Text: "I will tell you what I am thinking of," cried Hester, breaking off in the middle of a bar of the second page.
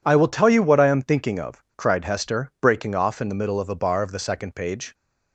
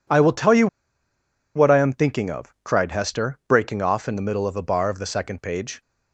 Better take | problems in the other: first | pauses between "you" and "what"; noticeable; at 0.6 s; 0.89 s long

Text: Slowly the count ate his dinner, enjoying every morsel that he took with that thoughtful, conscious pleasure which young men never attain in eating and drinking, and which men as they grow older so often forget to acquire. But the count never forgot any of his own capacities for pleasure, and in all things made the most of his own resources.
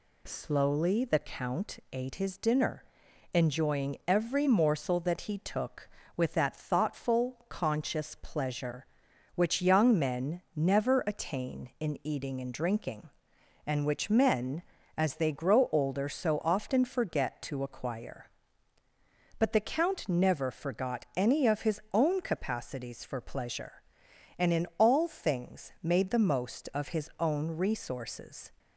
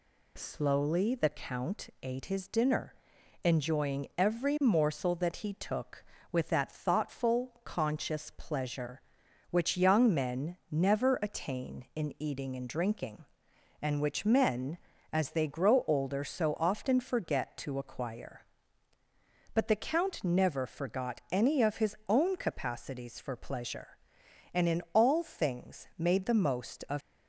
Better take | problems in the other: first | stops before "his own resources"; at 27.0 s

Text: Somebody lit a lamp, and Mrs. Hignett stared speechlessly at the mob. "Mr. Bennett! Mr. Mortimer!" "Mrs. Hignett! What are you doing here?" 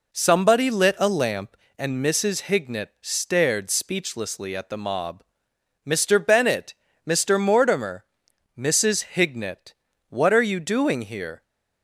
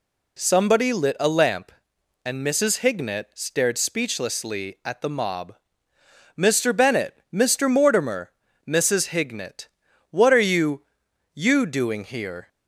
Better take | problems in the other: first | says "you" twice; at 11.3 s

